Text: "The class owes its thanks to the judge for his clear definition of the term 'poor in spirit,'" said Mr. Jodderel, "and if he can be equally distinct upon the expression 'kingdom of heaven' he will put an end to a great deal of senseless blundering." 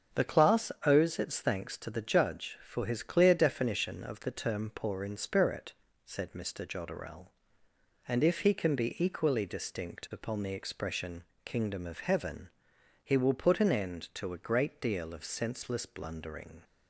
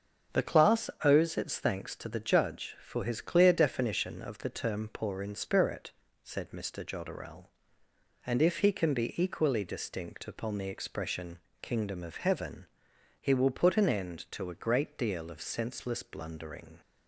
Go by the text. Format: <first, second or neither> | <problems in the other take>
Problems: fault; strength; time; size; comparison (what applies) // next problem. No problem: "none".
neither | starts louder than the rest; strong; the same in both // pauses between "expression" and "kingdom"; slight; the same in both // pauses between "heaven" and "he"; noticeable; the same in both